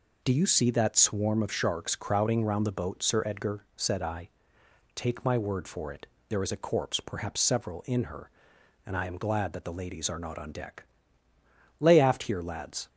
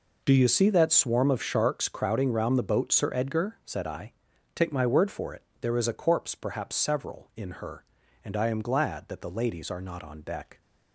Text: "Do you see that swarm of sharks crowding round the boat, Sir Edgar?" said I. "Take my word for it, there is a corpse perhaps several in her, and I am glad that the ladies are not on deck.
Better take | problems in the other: second | goes on to say "Lay aft here lads"; noticeable; from 11.8 s on; 1.0 s long

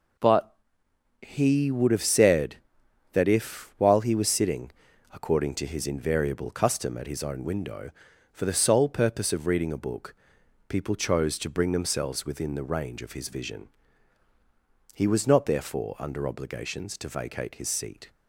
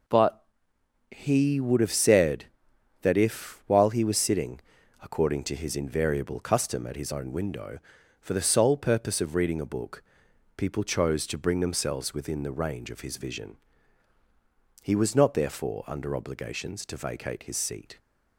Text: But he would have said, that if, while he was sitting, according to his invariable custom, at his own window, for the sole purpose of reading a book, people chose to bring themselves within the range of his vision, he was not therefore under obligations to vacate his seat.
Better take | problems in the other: neither | pauses between "But" and "he"; noticeable; the same in both

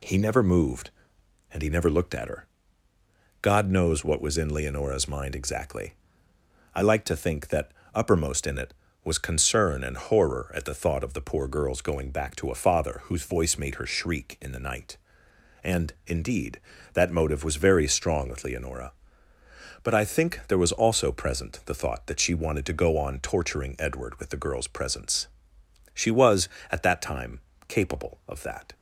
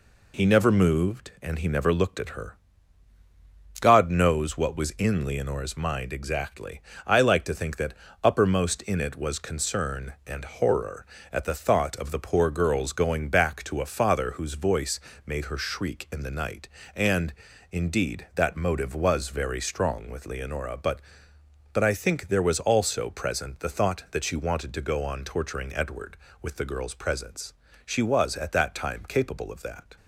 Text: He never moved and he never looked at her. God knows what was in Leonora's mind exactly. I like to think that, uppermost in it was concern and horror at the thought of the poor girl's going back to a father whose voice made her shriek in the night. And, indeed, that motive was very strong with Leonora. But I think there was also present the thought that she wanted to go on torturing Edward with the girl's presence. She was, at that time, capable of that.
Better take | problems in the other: first | pauses between "voice" and "made"; slight; at 14.9 s; 0.26 s long // says "But" twice; at 21.7 s

